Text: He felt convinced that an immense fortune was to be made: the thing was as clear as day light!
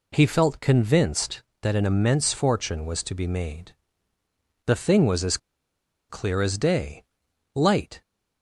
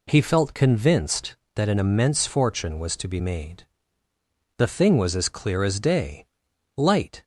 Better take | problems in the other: second | pauses between "as" and "clear"; noticeable; at 5.3 s; 0.72 s long // pauses between "day" and "light"; noticeable; at 7.0 s; 0.50 s long; noticeable in the second

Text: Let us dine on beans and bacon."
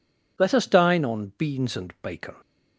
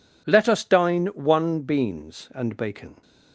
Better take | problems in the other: first | says "one" for "on"; at 1.0 s

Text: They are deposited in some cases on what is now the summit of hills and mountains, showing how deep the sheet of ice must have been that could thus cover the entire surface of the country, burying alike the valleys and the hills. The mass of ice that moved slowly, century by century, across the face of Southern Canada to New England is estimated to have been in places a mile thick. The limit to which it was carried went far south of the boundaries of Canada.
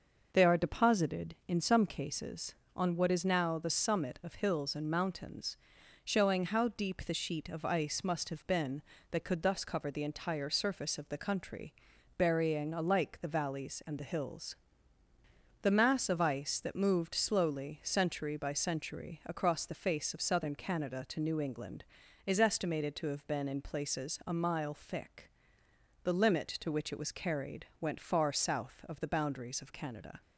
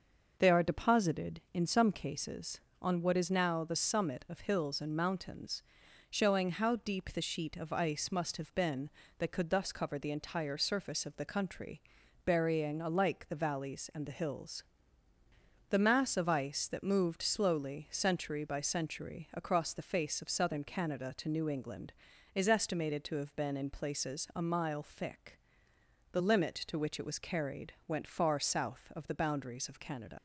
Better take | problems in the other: first | pauses between "carried" and "went"; slight; at 27.7 s; 0.16 s long; slight in the first // leaves "Canada" unfinished; at 30.1 s; 95 ms

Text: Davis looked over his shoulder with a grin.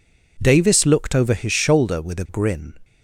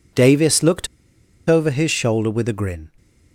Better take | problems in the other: first | pauses between "looked" and "over"; noticeable; at 0.8 s; 0.60 s long

